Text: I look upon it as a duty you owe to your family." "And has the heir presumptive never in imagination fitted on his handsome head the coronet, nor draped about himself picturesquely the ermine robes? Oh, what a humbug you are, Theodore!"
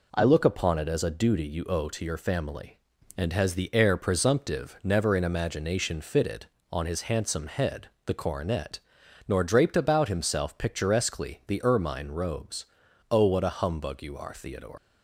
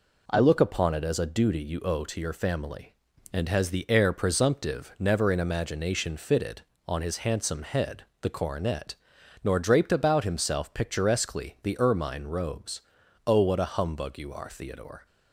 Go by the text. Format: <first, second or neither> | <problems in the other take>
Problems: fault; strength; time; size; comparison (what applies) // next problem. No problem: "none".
second | pauses between "head" and "the"; slight; at 7.8 s; 0.16 s long; slight in the second // leaves "Theodore" unfinished; at 14.7 s; 120 ms